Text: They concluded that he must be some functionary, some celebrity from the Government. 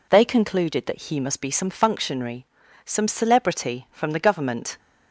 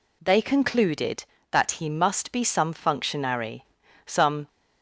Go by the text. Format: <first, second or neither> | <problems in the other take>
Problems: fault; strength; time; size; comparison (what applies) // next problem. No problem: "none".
first | stops before "celebrity from the Government"; at 4.4 s